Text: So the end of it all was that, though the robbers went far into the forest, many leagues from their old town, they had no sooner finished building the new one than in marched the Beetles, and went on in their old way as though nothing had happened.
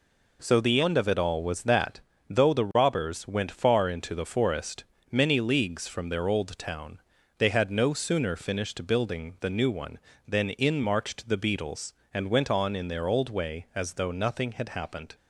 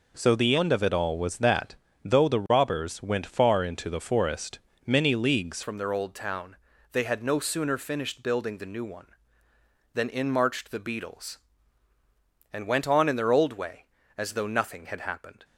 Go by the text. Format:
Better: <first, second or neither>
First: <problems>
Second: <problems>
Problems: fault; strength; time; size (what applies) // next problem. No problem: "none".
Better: first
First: none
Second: changes voice at "from"; from 5.6 s on; 9.8 s long